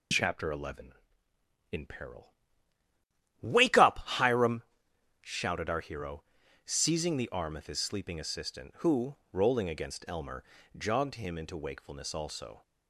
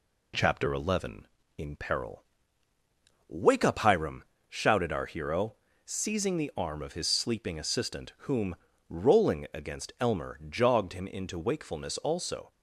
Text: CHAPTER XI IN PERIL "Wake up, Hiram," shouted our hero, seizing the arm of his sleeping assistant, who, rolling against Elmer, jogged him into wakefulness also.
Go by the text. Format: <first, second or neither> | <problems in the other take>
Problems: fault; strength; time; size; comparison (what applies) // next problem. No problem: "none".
first | pauses between "PERIL" and "Wake"; at 2.2 s; 1.0 s long; also in the first // says "whom" for "who"; at 8.2 s